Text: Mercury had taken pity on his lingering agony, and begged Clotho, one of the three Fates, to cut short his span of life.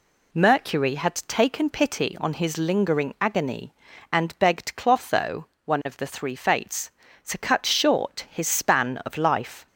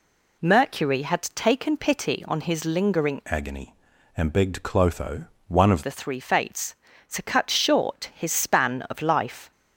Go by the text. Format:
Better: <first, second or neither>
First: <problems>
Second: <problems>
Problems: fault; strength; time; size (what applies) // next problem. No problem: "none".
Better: first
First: none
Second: changes voice from "agony" to "of"; from 3.2 to 5.8 s; 2.6 s long